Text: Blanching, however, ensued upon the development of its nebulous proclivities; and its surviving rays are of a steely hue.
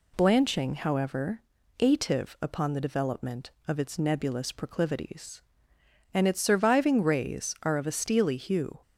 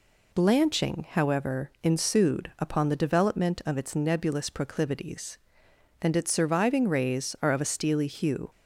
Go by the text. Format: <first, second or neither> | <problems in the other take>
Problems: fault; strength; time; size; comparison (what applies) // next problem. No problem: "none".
second | says "ative" for "ensued"; at 1.8 s